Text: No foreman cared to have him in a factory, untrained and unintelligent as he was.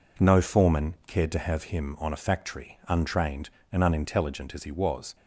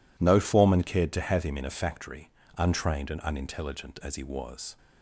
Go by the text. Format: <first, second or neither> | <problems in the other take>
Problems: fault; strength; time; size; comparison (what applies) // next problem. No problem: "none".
second | says "on" for "in"; at 1.9 s